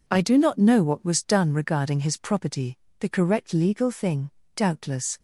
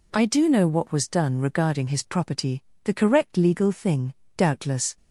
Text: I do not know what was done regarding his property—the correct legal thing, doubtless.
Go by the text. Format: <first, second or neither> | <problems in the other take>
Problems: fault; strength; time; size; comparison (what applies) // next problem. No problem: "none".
first | skips "not"; at 0.4 s